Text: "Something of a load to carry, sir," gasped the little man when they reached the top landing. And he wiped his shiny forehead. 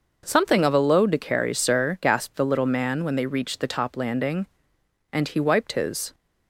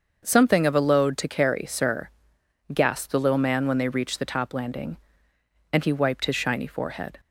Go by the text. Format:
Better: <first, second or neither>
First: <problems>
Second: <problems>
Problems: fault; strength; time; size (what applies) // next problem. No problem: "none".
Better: second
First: starts louder than the rest; noticeable; until 1.2 s; 6 dB // stops before "shiny forehead"; at 6.1 s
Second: starts louder than the rest; until 1.2 s; 6.5 dB